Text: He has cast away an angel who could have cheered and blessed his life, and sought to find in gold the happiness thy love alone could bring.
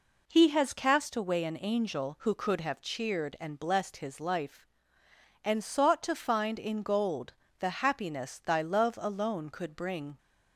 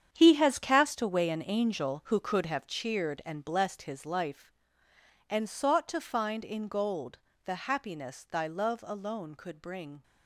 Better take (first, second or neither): first